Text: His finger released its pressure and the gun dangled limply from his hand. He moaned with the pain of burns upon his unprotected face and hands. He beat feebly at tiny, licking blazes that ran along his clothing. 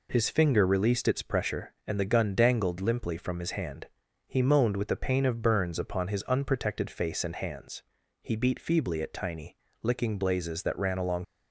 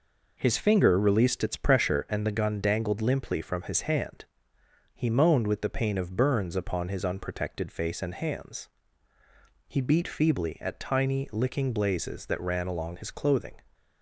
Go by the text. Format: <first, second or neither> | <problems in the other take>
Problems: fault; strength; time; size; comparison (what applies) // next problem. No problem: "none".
second | stops before "his clothing"; at 11.2 s